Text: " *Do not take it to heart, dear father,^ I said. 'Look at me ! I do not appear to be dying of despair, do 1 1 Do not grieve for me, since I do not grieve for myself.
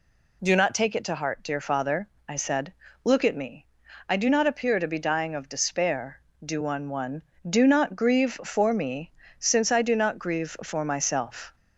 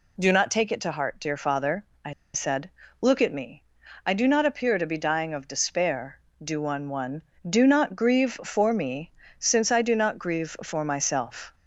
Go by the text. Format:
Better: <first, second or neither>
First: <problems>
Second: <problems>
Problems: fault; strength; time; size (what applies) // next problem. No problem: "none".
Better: first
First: none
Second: pauses between "I" and "said"; slight; at 2.1 s; 0.21 s long